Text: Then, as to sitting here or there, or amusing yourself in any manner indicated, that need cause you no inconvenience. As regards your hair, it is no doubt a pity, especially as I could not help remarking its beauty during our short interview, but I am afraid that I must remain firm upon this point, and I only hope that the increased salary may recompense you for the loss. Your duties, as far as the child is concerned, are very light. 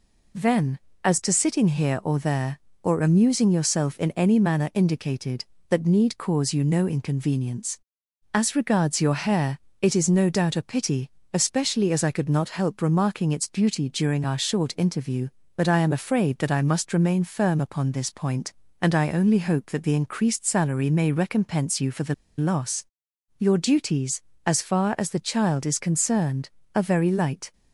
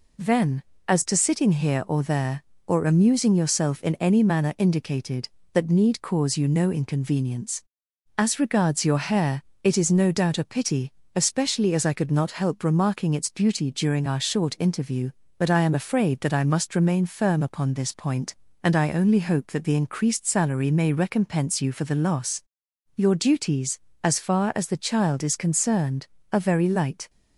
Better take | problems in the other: second | pauses between "the" and "loss"; slight; at 22.1 s; 0.23 s long

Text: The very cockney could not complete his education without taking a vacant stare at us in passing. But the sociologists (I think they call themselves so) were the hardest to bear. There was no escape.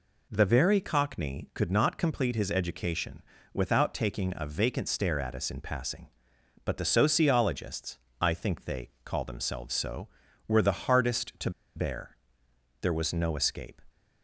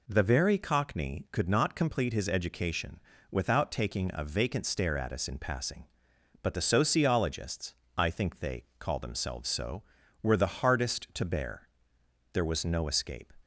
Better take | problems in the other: second | pauses between "education" and "without"; slight; at 3.2 s; 0.32 s long; slight in the second // pauses between "they" and "call"; slight; at 8.9 s; 0.16 s long; slight in the second // pauses between "to" and "bear"; slight; at 11.5 s; 0.25 s long

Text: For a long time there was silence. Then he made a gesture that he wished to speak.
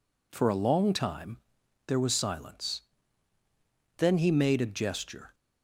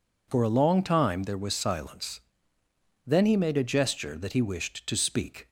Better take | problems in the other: second | pauses between "time" and "there"; noticeable; at 1.3 s; 0.50 s long // stops before "that he wished to speak"; at 5.3 s

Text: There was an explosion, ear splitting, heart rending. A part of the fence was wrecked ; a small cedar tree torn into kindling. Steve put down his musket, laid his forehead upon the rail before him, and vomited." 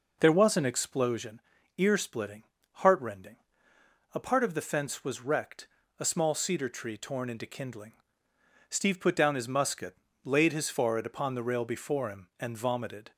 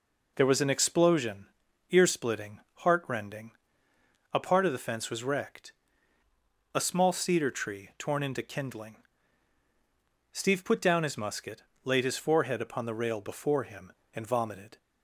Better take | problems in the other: neither | none

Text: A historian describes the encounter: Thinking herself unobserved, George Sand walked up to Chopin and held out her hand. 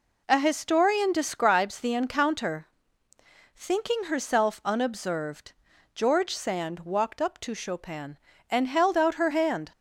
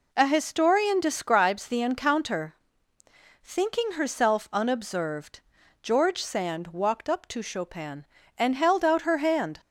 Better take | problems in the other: neither | none

